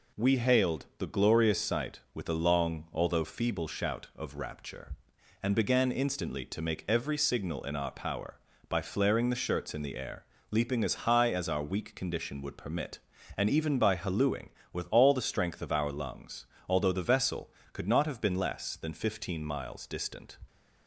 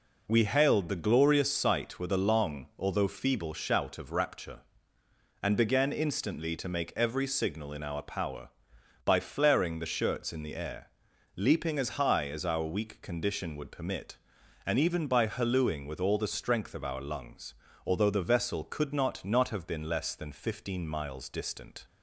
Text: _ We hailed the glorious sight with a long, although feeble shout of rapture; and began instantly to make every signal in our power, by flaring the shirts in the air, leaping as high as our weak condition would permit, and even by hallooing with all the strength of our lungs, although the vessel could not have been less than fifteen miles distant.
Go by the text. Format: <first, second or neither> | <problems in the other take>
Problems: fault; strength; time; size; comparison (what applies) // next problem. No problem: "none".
first | says "not" twice; at 19.2 s